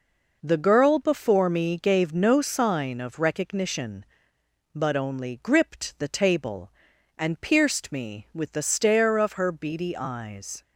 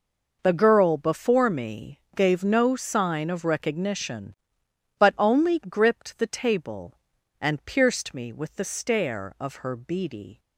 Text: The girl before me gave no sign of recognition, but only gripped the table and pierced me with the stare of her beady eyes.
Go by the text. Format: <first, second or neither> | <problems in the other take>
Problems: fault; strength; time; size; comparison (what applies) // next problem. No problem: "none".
first | pauses between "me" and "gave"; slight; at 1.9 s; 0.16 s long // stops before "eyes"; at 10.3 s